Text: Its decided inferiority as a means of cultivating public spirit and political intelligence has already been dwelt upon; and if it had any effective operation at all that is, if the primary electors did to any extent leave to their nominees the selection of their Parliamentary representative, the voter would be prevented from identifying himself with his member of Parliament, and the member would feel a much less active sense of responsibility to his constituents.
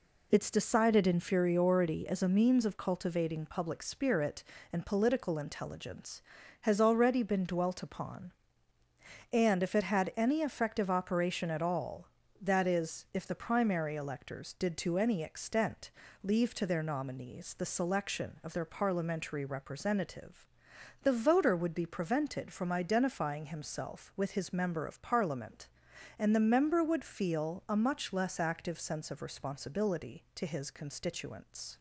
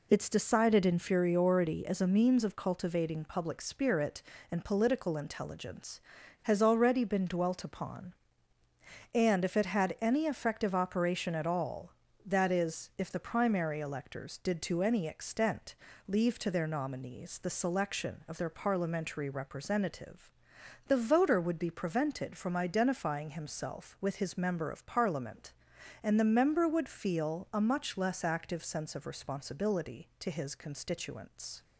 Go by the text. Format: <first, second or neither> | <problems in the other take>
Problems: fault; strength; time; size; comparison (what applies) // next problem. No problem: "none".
neither | pauses between "extent" and "leave"; slight; the same in both